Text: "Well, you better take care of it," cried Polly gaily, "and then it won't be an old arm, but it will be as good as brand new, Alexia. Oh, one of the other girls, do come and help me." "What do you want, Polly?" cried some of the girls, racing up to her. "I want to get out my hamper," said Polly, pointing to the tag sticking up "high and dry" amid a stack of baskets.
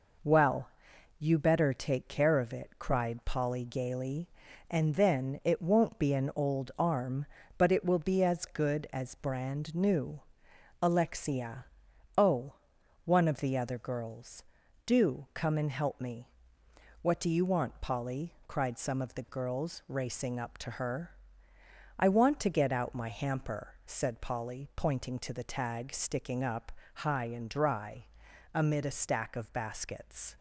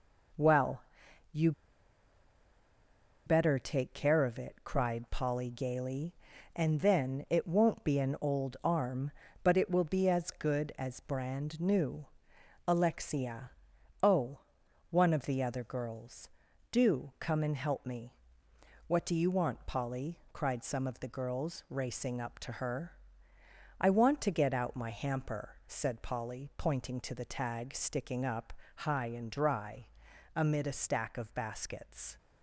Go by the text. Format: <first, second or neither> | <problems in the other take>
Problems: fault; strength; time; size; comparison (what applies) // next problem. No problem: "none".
first | pauses between "you" and "better"; strong; at 1.5 s; 1.7 s long // pauses between "up" and "high"; slight; at 28.5 s; 0.24 s long; slight in the first // pauses between "dry" and "amid"; noticeable; at 29.8 s; 0.48 s long; noticeable in the first